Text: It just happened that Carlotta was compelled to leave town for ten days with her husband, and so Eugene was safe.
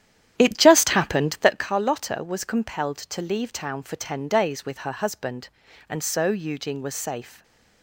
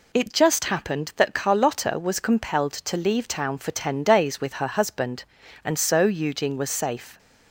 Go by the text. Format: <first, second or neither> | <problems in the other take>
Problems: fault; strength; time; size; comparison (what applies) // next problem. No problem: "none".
second | starts louder than the rest; strong; until 1.7 s; 10.5 dB // stays silent after the last word; slight; from 7.3 s on; 0.5 s long